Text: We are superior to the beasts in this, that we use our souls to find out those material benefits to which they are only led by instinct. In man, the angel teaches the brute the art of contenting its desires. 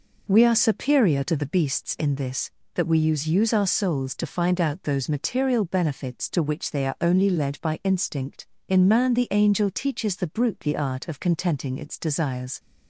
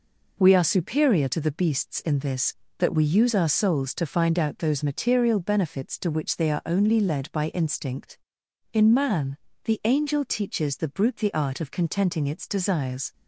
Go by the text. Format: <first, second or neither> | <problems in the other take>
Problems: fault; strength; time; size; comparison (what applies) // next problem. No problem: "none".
second | says "use" twice; at 3.2 s